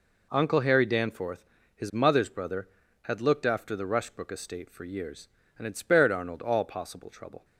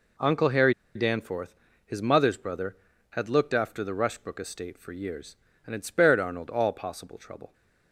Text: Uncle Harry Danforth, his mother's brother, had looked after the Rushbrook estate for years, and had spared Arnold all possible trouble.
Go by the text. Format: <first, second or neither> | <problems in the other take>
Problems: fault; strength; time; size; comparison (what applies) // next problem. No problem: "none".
first | pauses between "Harry" and "Danforth"; slight; at 0.7 s; 0.22 s long